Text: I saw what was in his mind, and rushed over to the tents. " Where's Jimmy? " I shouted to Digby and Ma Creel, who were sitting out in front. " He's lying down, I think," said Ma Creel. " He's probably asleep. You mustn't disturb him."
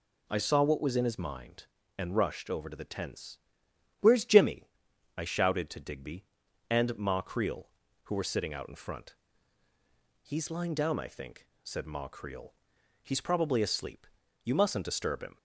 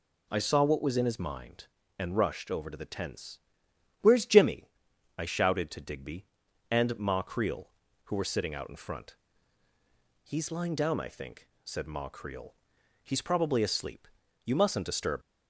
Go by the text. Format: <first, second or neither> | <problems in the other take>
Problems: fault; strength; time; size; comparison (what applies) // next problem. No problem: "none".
first | stops before "him"; at 15.2 s